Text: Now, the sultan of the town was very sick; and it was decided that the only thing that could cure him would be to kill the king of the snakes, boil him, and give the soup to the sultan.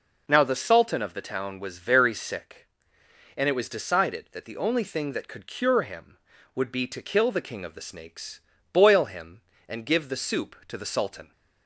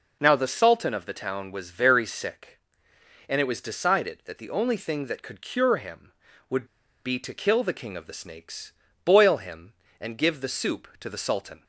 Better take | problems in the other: first | pauses between "would" and "be"; at 6.6 s; 0.40 s long

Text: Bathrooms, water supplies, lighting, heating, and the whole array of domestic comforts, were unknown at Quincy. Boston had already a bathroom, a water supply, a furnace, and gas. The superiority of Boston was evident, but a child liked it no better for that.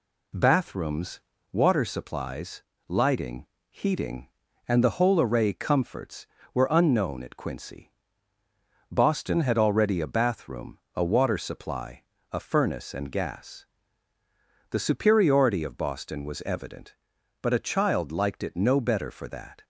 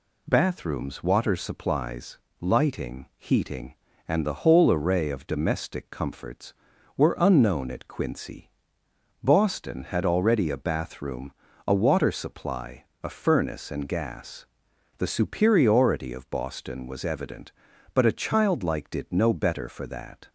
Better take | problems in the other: second | skips "of domestic"; at 5.5 s

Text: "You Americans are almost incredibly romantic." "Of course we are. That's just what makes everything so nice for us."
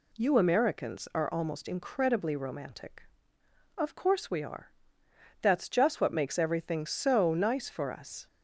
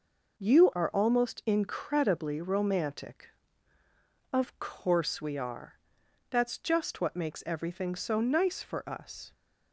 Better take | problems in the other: first | skips "Americans"; at 0.7 s

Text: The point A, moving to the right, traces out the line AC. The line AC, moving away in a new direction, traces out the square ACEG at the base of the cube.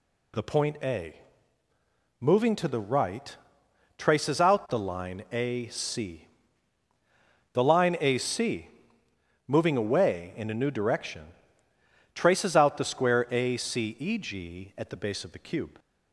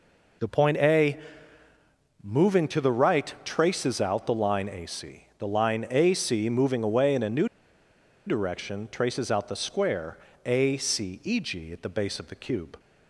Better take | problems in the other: first | pauses between "new" and "direction"; noticeable; at 7.4 s; 0.80 s long // pauses between "square" and "ACEG"; slight; at 10.1 s; 0.28 s long

